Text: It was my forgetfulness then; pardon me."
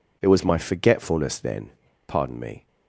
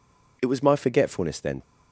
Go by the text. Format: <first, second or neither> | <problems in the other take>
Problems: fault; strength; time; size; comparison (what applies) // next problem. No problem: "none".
first | stops before "pardon me"; at 1.6 s